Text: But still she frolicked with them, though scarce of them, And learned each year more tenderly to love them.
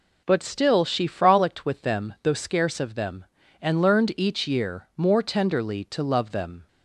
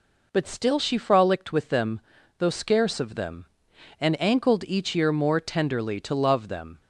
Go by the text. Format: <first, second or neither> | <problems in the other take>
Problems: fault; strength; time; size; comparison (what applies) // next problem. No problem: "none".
first | says "ankled" for "learned"; at 4.2 s